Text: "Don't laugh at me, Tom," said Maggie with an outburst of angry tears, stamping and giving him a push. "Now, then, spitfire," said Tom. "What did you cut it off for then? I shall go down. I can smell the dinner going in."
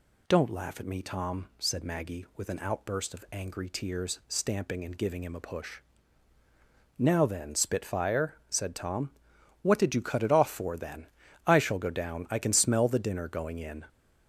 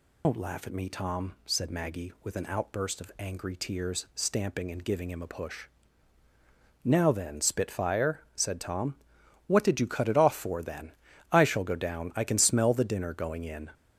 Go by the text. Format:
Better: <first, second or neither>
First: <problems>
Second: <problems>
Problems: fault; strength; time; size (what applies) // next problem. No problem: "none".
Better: first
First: none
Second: loses the start of "Don't"; at 0.2 s; 105 ms